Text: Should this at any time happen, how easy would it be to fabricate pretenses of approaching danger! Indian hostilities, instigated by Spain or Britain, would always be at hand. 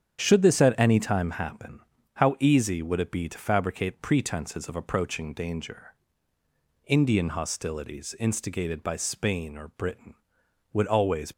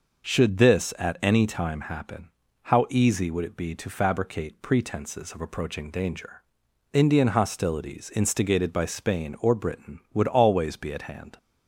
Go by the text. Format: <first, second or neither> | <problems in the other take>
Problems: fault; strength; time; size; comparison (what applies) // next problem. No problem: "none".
second | starts louder than the rest; strong; until 1.2 s; 8.5 dB // stops before "be at hand"; at 11.3 s